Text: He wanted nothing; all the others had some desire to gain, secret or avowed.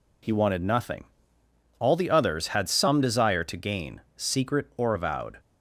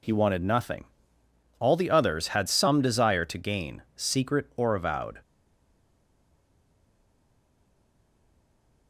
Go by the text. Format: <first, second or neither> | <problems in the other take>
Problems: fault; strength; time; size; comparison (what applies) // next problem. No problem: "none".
first | stays silent after the last word; strong; from 5.2 s on; 3.6 s long